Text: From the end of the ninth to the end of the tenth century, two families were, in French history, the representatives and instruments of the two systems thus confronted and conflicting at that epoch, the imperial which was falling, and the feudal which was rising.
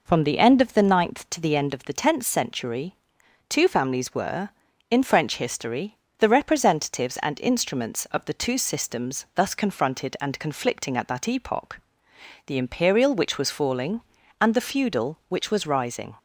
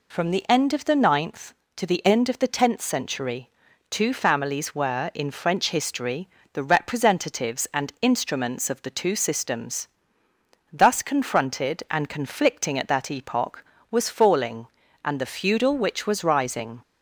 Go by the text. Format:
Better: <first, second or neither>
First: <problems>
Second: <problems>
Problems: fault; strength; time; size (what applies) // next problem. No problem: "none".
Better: first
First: none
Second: pauses between "systems" and "thus"; noticeable; at 9.8 s; 0.86 s long // skips "the imperial which"; at 13.7 s